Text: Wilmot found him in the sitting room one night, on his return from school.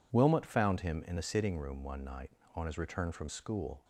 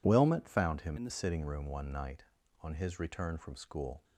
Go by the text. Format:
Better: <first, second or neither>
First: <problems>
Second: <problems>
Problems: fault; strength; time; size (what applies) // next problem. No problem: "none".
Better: first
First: none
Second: changes voice from "in" to "the"; from 0.9 to 1.1 s; 0.2 s long